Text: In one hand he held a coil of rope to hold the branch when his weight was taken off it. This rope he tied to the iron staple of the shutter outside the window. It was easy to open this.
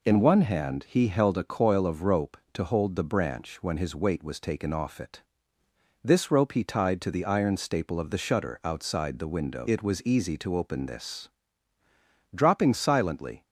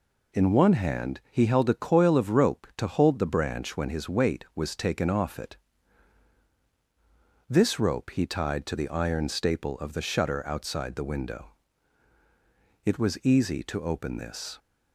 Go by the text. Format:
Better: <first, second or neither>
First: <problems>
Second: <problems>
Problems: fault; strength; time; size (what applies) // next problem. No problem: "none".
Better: second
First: goes on to say "Dropping silently"; noticeable; from 12.3 s on; 1.1 s long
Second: none